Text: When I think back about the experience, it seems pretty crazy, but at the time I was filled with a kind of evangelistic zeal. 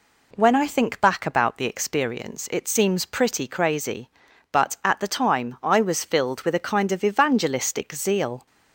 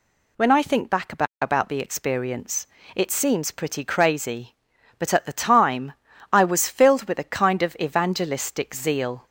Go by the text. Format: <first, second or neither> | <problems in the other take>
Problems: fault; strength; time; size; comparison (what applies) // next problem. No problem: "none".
first | says "about" twice; at 1.4 s // pauses between "time" and "I"; at 5.9 s; 0.40 s long